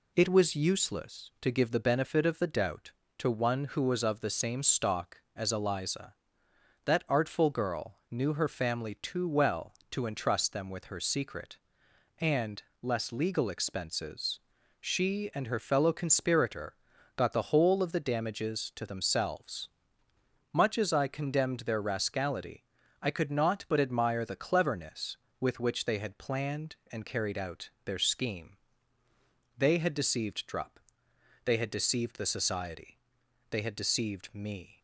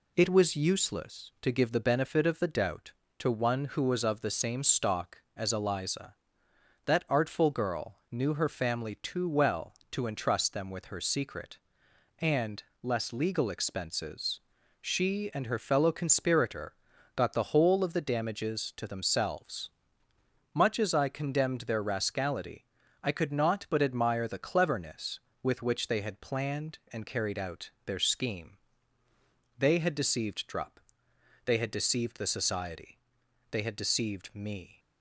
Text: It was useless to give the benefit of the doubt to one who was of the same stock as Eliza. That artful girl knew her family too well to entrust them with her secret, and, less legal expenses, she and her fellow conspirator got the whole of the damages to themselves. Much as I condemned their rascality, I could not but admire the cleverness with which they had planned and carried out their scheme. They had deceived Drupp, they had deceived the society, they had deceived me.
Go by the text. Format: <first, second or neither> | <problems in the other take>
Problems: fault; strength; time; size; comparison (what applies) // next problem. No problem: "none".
neither | pauses between "girl" and "knew"; slight; the same in both // pauses between "conspirator" and "got"; the same in both // pauses between "out" and "their"; slight; the same in both